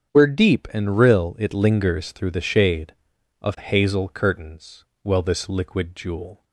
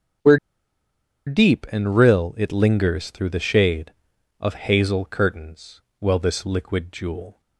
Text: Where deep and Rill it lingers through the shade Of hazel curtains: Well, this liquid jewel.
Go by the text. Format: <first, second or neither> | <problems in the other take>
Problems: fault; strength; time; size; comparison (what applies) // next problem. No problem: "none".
first | starts louder than the rest; strong; until 2.1 s; 7.5 dB; strong in the first // pauses between "Where" and "deep"; noticeable; at 0.3 s; 0.90 s long